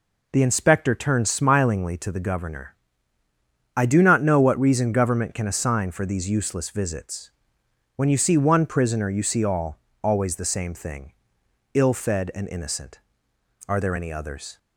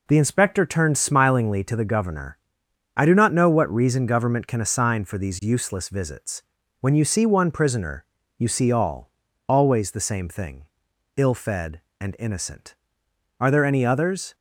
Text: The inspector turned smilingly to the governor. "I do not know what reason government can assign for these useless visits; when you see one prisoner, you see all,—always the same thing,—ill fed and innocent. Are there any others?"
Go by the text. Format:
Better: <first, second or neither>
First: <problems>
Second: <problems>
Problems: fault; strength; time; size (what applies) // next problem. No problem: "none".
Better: neither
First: none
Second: none